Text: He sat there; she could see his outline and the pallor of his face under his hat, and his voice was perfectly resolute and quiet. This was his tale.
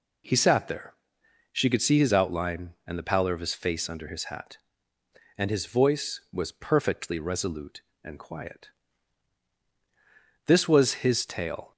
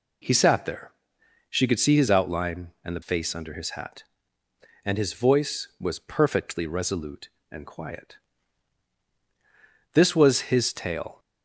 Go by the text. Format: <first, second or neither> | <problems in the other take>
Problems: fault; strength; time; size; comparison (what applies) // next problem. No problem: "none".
first | skips "pallor of his"; at 3.0 s